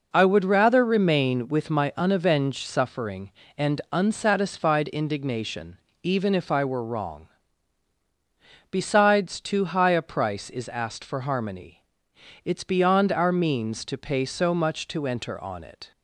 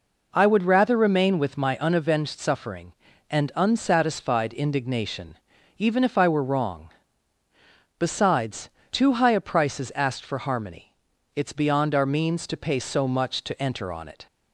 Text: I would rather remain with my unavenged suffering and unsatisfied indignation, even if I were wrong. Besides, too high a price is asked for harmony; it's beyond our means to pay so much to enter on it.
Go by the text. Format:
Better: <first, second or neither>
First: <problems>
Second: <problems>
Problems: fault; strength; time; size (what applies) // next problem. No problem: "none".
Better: neither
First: none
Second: none